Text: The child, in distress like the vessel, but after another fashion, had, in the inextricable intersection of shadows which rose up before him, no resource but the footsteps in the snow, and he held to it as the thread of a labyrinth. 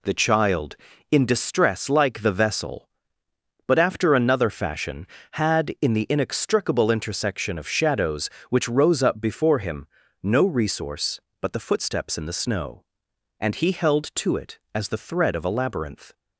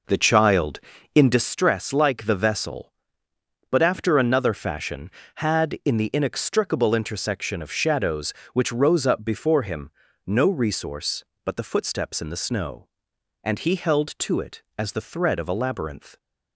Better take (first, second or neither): first